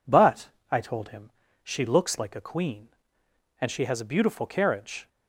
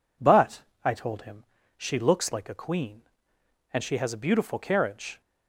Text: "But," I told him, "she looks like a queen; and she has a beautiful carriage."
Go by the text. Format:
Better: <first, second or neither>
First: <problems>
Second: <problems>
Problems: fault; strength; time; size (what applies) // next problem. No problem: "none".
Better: neither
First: none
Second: none